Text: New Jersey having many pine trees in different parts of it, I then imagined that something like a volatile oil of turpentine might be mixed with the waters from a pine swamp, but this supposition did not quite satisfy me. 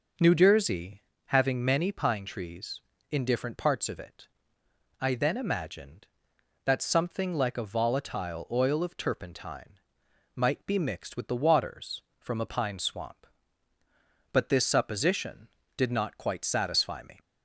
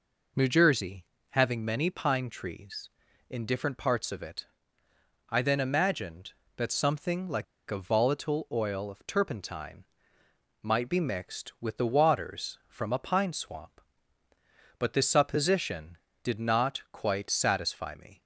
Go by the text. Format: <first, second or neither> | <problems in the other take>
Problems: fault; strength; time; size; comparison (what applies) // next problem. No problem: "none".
first | pauses between "Jersey" and "having"; slight; at 1.0 s; 0.24 s long; slight in the first // pauses between "like" and "a"; slight; at 7.4 s; 0.25 s long // pauses between "turpentine" and "might"; noticeable; at 9.8 s; 0.78 s long; noticeable in the first